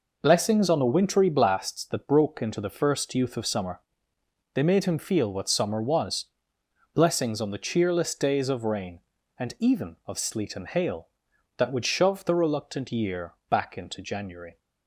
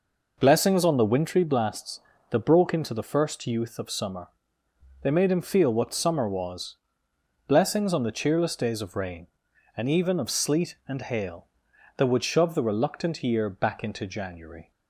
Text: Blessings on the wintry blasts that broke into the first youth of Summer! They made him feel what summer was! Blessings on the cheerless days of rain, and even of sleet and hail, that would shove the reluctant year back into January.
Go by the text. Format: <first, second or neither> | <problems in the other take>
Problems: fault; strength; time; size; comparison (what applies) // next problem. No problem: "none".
neither | none